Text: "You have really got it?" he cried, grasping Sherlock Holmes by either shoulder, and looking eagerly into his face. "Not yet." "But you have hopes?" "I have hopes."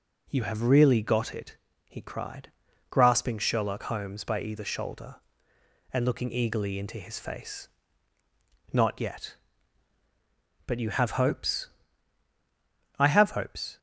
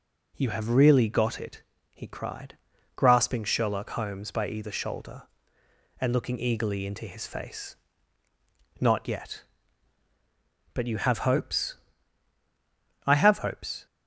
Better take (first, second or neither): neither